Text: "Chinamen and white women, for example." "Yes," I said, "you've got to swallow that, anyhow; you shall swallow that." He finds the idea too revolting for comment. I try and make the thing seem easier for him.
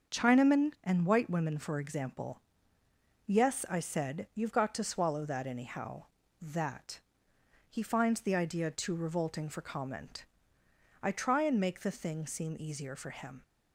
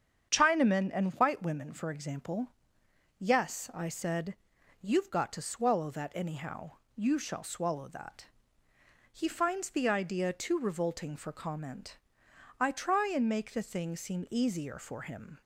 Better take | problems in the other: second | starts louder than the rest; until 1.2 s; 7 dB; strong in the second // skips "you shall swallow"; at 6.2 s

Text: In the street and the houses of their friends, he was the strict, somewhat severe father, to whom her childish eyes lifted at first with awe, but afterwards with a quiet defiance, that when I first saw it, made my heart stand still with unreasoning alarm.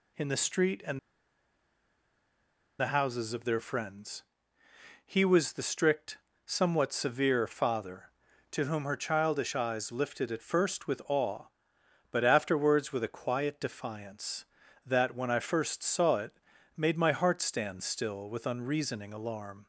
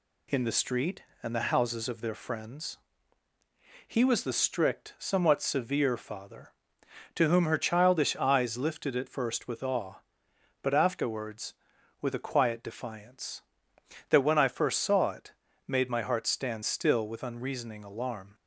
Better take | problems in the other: second | pauses between "and" and "the"; strong; at 0.9 s; 1.8 s long

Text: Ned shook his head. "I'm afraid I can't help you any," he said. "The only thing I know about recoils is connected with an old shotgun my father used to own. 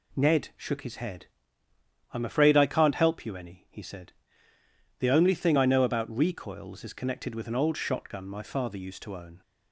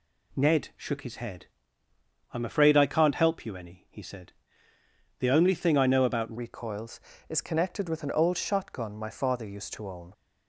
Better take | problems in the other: first | changes voice at "recoils"; from 6.3 s on; 3.8 s long

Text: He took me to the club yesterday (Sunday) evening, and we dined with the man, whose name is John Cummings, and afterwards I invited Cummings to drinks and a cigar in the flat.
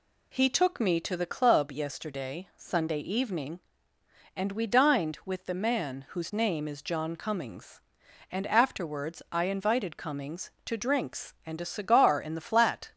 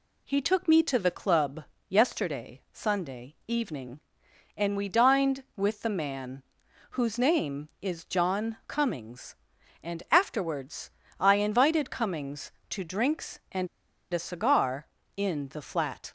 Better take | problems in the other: first | pauses between "club" and "yesterday"; slight; at 1.6 s; 0.22 s long // pauses between "afterwards" and "I"; slight; at 10.8 s; 0.32 s long // pauses between "and" and "a"; at 13.6 s; 0.44 s long

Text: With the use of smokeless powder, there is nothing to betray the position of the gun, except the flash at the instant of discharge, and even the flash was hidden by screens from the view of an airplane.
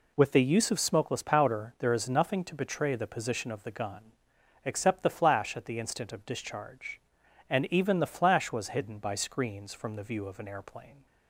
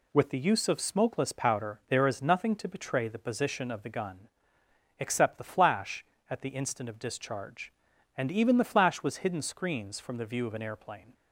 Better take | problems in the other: first | skips "by"; at 9.4 s

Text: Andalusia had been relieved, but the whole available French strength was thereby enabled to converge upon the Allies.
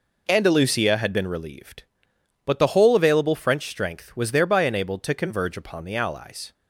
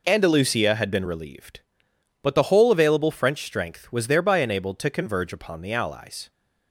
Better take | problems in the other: neither | none

